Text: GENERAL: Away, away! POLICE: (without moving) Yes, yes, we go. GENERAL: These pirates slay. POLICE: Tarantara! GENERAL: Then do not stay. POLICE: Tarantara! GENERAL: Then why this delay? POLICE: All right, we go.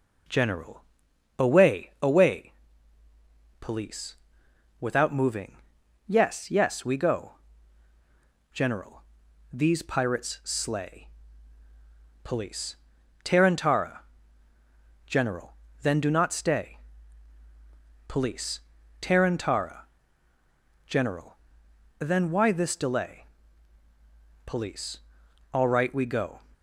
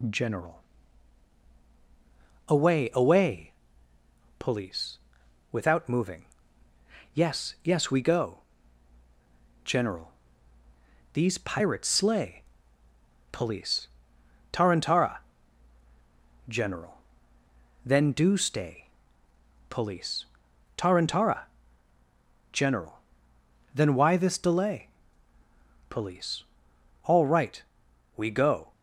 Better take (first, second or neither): first